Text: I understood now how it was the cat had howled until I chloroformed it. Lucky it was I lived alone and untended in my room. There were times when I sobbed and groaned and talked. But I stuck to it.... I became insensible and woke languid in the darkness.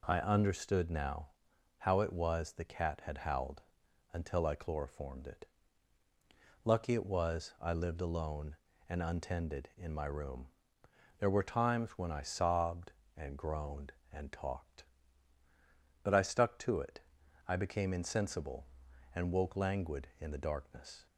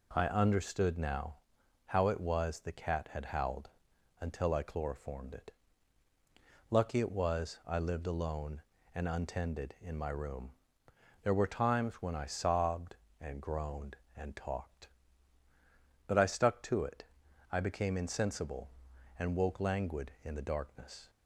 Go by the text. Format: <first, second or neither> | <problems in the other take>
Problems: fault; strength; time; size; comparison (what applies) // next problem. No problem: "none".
neither | pauses between "now" and "how"; noticeable; the same in both // pauses between "howled" and "until"; noticeable; the same in both